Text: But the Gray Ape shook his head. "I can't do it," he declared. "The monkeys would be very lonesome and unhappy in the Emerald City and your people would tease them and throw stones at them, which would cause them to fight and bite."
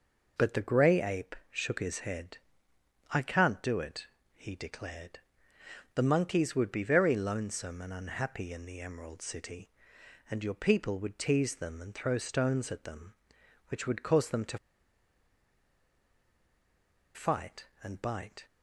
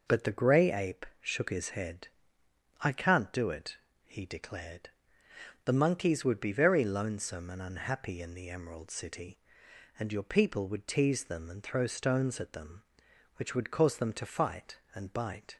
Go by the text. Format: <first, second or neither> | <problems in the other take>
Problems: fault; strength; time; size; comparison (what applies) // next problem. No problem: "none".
second | pauses between "to" and "fight"; strong; at 14.5 s; 2.5 s long